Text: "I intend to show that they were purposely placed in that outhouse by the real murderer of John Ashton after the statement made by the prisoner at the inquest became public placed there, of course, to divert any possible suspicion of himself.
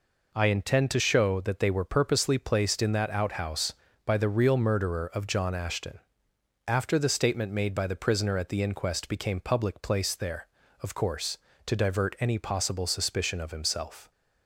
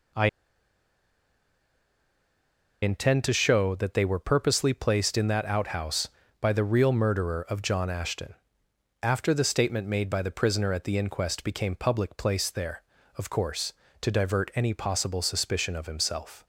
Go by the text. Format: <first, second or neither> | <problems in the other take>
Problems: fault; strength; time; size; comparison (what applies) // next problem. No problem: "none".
first | pauses between "I" and "intend"; strong; at 0.2 s; 2.5 s long // pauses between "Ashton" and "after"; noticeable; at 8.3 s; 0.68 s long; noticeable in the first